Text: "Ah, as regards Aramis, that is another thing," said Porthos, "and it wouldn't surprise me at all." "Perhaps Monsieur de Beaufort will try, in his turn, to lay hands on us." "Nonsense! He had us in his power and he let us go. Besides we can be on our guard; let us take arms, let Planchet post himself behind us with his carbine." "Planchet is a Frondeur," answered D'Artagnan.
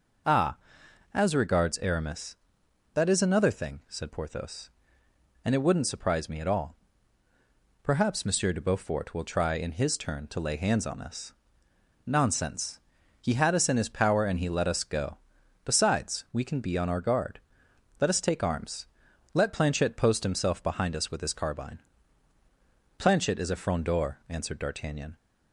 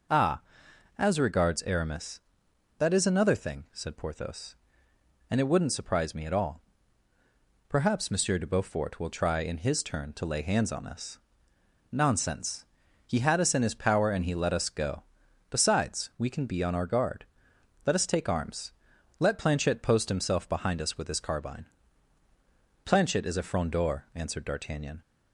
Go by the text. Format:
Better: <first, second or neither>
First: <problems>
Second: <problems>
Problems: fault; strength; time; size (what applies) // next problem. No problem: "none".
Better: neither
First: none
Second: none